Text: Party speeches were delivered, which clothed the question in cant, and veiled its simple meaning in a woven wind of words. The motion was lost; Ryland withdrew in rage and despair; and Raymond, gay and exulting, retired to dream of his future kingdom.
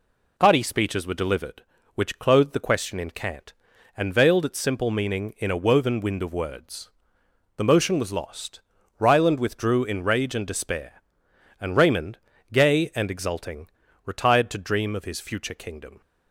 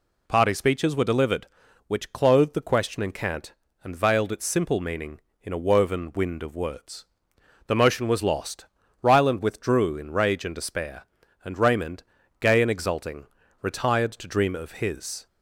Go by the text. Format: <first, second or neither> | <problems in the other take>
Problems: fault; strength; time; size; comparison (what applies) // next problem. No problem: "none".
first | stops before "future kingdom"; at 15.2 s